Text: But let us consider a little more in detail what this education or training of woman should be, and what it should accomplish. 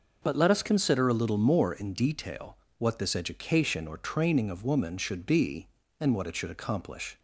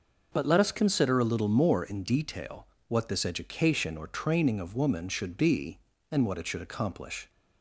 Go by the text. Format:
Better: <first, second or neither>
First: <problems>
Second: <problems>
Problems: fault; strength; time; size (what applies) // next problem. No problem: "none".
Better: neither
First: pauses between "detail" and "what"; slight; at 2.5 s; 0.22 s long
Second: pauses between "detail" and "what"; slight; at 2.6 s; 0.22 s long